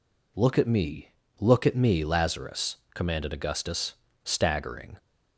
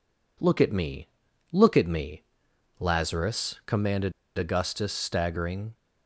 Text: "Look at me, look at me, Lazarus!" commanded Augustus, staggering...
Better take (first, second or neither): first